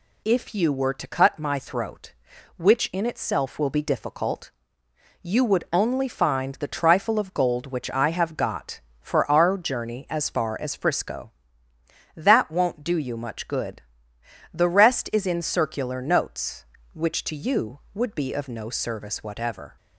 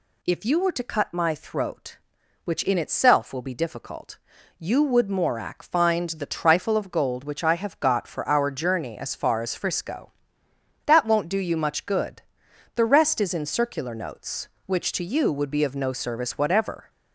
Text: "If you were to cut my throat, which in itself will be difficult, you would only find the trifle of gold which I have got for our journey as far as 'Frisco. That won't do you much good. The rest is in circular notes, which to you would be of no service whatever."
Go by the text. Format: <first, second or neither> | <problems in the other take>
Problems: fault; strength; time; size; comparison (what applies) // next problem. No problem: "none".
first | says "morak" for "only"; at 5.0 s